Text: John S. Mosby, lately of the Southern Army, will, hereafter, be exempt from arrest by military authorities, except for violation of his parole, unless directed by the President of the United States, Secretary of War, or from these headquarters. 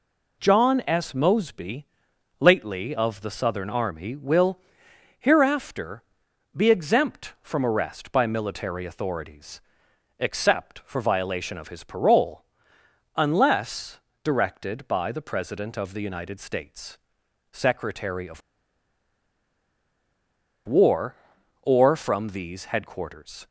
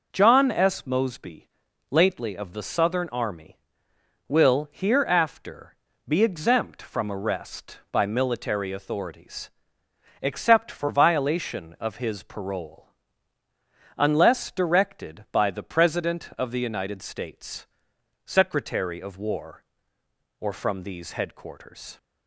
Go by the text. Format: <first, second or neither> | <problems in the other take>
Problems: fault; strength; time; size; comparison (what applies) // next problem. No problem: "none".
second | pauses between "unless" and "directed"; slight; at 13.9 s; 0.24 s long // pauses between "of" and "War"; strong; at 18.4 s; 2.2 s long